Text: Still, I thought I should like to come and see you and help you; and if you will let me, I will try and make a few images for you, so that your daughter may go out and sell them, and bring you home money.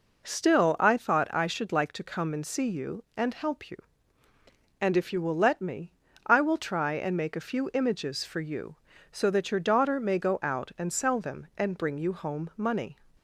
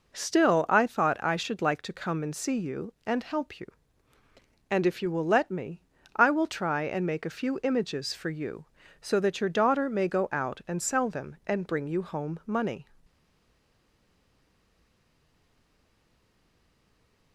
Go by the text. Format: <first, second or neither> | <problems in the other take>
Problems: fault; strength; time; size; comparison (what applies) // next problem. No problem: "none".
first | stays silent after the last word; strong; from 13.0 s on; 4.3 s long